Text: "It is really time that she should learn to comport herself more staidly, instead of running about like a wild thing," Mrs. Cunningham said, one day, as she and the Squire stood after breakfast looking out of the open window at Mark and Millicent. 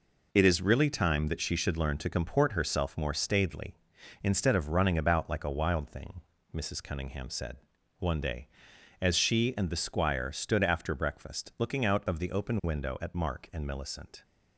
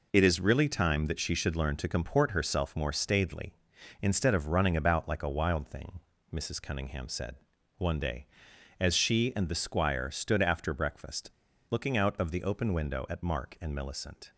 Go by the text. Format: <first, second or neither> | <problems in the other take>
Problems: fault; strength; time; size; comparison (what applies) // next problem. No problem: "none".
first | pauses between "breakfast" and "looking"; at 11.2 s; 0.39 s long